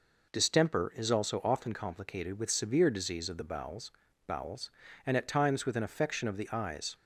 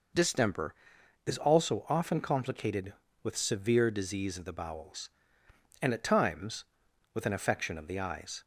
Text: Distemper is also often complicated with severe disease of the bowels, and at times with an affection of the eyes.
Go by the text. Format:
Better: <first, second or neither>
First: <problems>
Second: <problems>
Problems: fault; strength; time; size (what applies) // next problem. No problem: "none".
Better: second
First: says "bowels" twice; at 4.2 s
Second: none